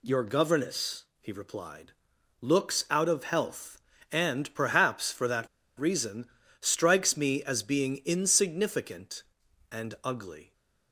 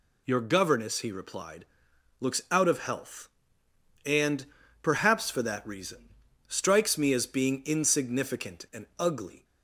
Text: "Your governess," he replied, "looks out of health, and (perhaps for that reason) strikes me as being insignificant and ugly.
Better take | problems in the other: second | pauses between "that" and "reason"; slight; at 5.4 s; 0.30 s long

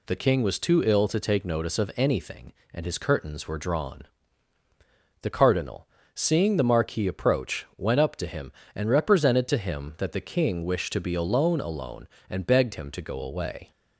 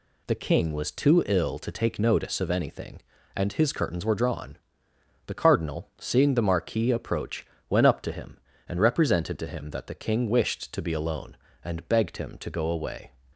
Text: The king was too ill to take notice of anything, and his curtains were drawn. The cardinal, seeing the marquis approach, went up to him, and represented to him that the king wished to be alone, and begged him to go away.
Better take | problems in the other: second | says "alone" twice; at 11.6 s

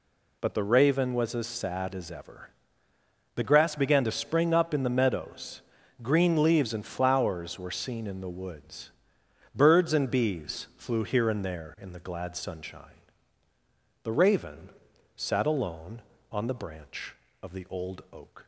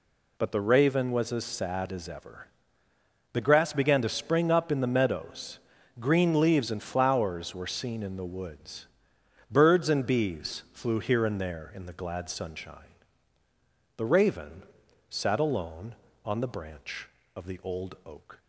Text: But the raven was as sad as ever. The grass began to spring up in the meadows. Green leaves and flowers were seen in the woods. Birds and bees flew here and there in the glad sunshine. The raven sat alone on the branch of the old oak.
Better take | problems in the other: neither | pauses between "raven" and "sat"; noticeable; the same in both

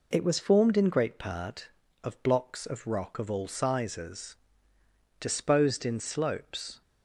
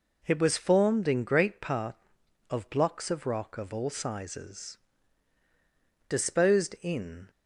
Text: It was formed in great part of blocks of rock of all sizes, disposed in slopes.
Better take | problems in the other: first | stops before "slopes"; at 7.2 s

